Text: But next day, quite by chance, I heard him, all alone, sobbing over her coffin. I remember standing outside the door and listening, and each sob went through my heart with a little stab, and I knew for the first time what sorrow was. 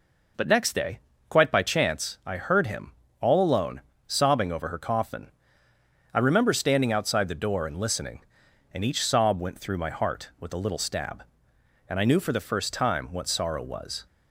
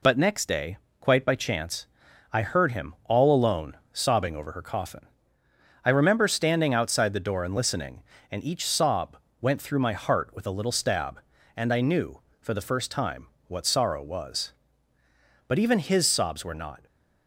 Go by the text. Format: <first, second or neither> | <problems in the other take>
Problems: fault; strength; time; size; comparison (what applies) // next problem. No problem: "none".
first | pauses between "sob" and "went"; slight; at 9.1 s; 0.24 s long // pauses between "time" and "what"; slight; at 13.2 s; 0.20 s long // goes on to say "But even his sobs were not"; from 15.4 s on; 1.3 s long